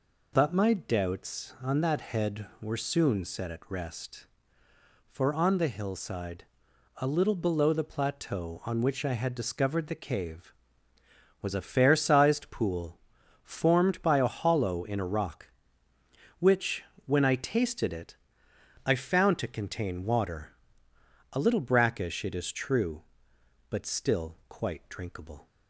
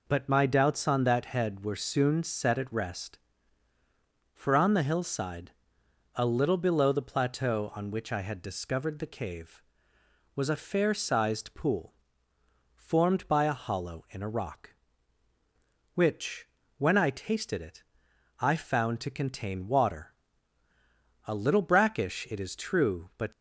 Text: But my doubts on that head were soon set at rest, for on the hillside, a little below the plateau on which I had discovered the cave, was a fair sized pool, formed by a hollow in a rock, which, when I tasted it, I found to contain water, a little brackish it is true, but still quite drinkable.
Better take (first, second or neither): first